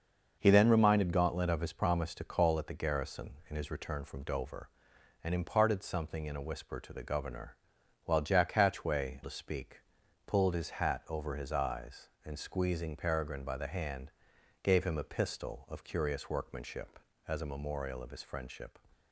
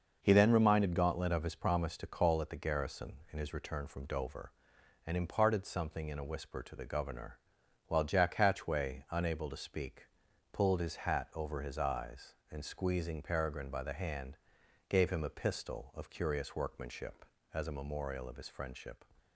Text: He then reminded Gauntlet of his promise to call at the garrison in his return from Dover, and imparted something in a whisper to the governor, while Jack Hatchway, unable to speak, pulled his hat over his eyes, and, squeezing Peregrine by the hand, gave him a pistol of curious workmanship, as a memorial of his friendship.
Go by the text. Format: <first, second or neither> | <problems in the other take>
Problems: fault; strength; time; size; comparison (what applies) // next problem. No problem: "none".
second | starts louder than the rest; until 1.4 s; 6 dB; noticeable in the second // skips "unable"; at 9.2 s